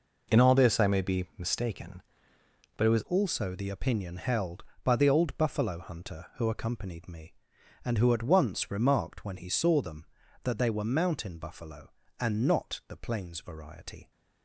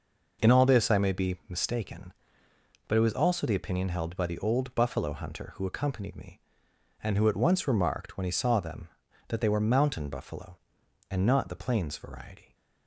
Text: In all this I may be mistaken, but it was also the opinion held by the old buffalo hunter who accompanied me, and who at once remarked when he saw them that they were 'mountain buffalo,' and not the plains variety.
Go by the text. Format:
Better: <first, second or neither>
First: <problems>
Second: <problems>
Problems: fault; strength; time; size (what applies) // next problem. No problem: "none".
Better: second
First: changes voice at "also"; from 3.0 s on; 11.1 s long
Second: none